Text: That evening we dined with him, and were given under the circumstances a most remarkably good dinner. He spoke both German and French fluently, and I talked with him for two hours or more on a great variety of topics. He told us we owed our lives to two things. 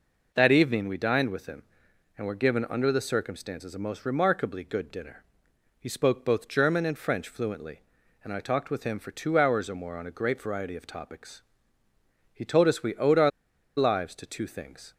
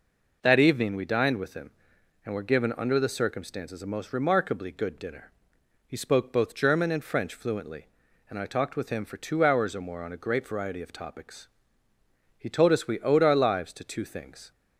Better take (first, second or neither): second